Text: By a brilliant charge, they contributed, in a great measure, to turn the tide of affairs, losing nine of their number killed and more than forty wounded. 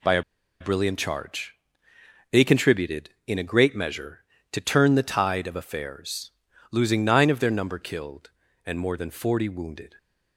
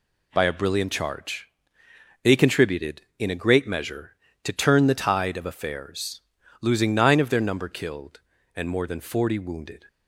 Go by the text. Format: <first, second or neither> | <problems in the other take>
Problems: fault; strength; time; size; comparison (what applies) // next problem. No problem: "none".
second | pauses between "a" and "brilliant"; at 0.2 s; 0.38 s long